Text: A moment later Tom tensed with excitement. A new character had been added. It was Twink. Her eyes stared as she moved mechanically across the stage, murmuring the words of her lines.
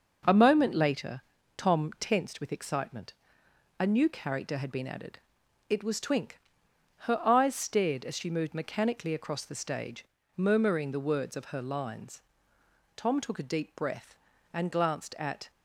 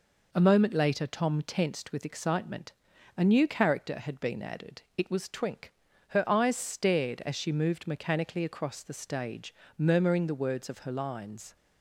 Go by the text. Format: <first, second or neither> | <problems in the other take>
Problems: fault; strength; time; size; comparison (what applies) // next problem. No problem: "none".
second | pauses between "later" and "Tom"; at 1.1 s; 0.38 s long // goes on to say "Tom took a deep breath and glanced at"; strong; from 12.9 s on; 2.5 s long